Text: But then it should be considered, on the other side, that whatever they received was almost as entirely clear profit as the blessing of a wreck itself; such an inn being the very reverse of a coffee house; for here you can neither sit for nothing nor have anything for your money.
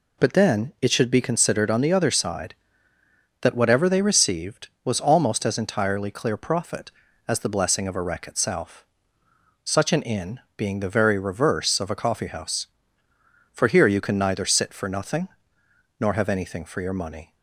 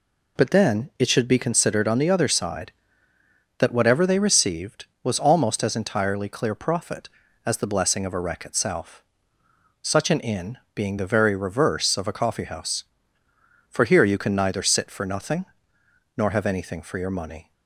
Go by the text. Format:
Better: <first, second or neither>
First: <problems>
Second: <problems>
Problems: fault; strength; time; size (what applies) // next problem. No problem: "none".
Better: neither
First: pauses between "inn" and "being"; slight; at 10.3 s; 0.16 s long // pauses between "nothing" and "nor"; noticeable; at 15.2 s; 0.72 s long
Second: pauses between "inn" and "being"; slight; at 10.5 s; 0.16 s long // pauses between "nothing" and "nor"; noticeable; at 15.4 s; 0.72 s long